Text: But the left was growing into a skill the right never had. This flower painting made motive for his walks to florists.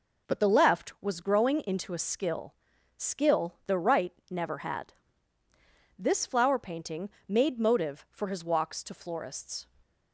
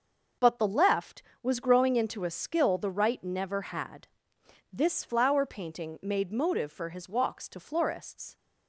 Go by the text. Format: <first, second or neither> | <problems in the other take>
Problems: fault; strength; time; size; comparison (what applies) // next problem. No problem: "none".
second | says "skill" twice; at 2.9 s // pauses between "right" and "never"; slight; at 4.1 s; 0.18 s long // pauses between "painting" and "made"; slight; at 7.0 s; 0.18 s long